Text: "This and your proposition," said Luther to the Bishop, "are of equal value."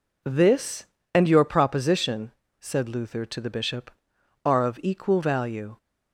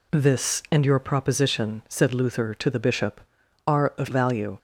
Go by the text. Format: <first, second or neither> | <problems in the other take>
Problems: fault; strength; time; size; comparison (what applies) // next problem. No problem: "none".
first | skips "equal"; at 4.0 s